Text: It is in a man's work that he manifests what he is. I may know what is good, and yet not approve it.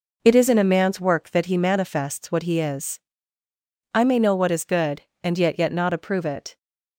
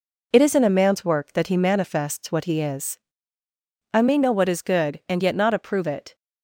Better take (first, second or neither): second